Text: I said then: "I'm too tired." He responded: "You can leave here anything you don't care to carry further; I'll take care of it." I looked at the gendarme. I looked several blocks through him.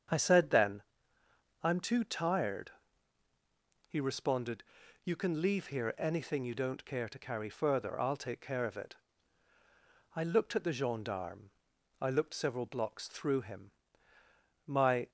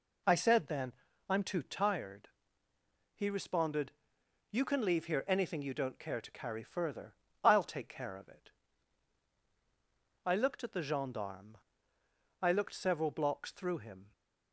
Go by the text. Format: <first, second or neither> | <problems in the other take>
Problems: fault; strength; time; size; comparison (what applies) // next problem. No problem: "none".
second | starts louder than the rest; strong; until 1.9 s; 7.5 dB // goes on to say "My"; slight; from 14.6 s on; 0.44 s long